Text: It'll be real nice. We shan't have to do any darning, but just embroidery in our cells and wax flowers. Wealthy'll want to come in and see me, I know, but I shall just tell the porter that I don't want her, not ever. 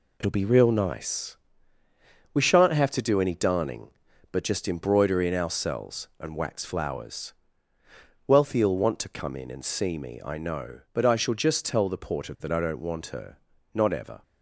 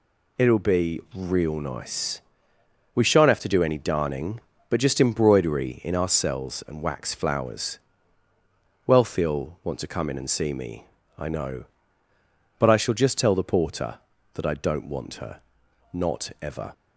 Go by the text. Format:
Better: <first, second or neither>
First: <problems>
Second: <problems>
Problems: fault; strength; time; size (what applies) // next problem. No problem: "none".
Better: neither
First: none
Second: none